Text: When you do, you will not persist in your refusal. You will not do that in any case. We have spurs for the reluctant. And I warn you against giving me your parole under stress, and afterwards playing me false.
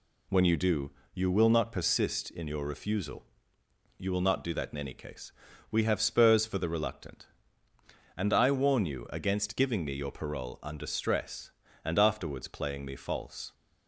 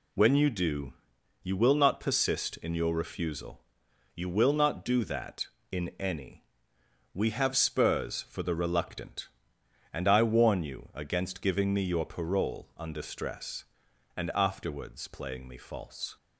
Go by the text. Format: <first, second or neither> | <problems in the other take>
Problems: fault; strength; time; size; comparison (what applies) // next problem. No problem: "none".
first | skips "case"; at 6.7 s